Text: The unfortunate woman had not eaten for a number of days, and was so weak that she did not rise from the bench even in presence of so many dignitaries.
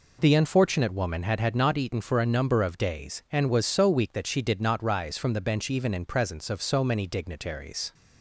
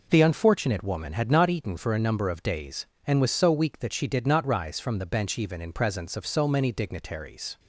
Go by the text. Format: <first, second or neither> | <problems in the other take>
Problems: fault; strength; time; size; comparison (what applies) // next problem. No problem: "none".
second | says "had" twice; at 1.3 s